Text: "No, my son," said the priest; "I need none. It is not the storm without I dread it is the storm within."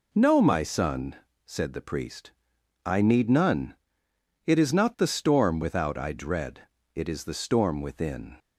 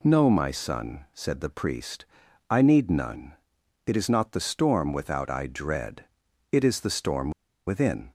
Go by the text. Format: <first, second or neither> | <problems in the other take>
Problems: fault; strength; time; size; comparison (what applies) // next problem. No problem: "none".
first | pauses between "dread" and "it"; at 6.0 s; 0.44 s long; slight in the first // pauses between "storm" and "within"; at 7.2 s; 0.37 s long